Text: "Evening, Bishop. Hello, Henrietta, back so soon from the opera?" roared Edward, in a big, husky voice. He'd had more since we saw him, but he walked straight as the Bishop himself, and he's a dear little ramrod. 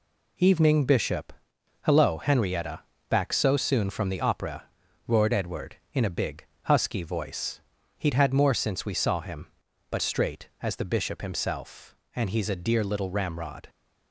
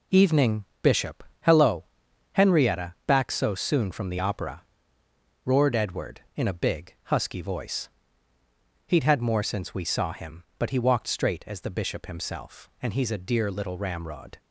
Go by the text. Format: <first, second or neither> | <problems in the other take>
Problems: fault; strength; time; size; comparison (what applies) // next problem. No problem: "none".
second | skips "he walked"; at 10.0 s